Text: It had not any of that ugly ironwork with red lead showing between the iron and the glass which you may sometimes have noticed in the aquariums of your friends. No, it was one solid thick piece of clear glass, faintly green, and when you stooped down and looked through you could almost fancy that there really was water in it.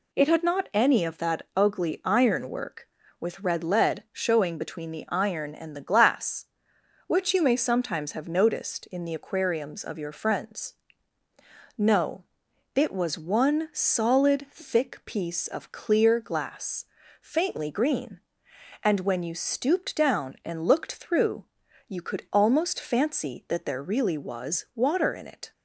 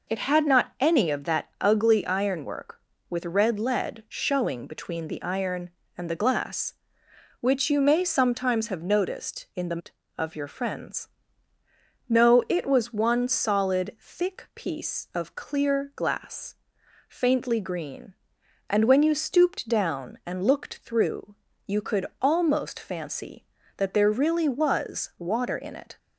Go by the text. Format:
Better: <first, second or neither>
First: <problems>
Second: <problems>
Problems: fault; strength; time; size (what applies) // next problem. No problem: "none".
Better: first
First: pauses between "through" and "you"; at 21.4 s; 0.42 s long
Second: skips "aquariums"; at 9.9 s // pauses between "through" and "you"; slight; at 21.3 s; 0.32 s long